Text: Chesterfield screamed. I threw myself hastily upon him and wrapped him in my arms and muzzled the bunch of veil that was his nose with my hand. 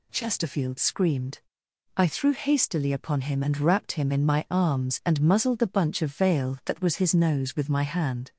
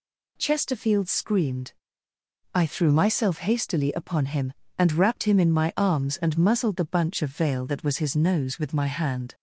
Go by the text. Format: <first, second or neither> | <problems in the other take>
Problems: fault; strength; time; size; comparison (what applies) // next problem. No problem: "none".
second | skips "myself"; at 2.3 s